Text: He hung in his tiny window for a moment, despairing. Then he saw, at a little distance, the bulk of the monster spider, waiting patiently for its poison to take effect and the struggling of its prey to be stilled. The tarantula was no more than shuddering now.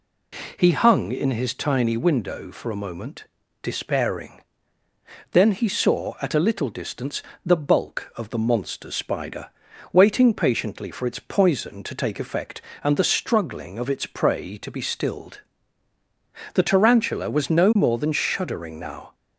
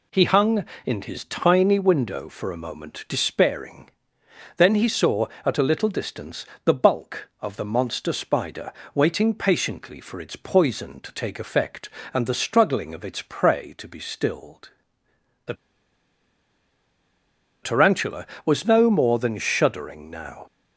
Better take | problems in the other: first | pauses between "The" and "tarantula"; strong; at 15.5 s; 2.0 s long

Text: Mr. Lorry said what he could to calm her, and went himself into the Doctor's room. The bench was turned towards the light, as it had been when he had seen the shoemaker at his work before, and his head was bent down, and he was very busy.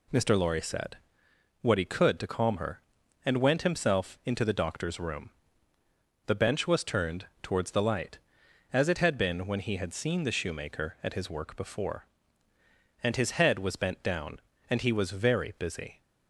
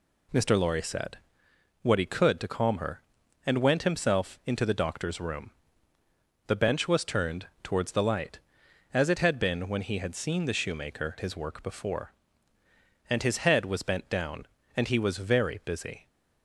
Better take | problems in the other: first | pauses between "said" and "what"; noticeable; at 1.1 s; 0.64 s long; noticeable in the first // pauses between "turned" and "towards"; slight; at 7.4 s; 0.18 s long; slight in the first // skips "at"; at 11.1 s

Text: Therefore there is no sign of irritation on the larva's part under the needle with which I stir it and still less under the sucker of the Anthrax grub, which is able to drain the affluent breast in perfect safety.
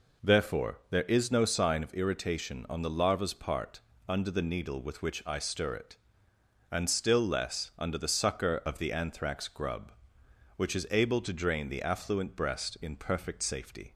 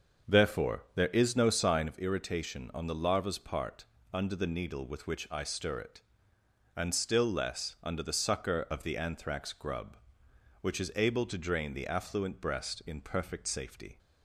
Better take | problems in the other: first | starts louder than the rest; until 2.0 s; 6.5 dB // pauses between "part" and "under"; slight; at 3.8 s; 0.28 s long; slight in the first

